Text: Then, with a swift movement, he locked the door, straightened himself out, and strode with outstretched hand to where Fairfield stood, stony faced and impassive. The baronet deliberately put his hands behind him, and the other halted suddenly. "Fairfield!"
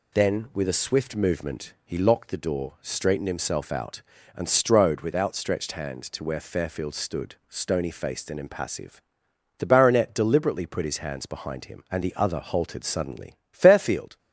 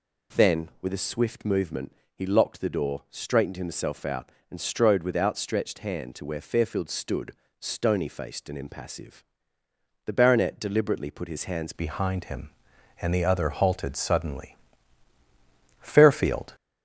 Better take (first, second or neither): first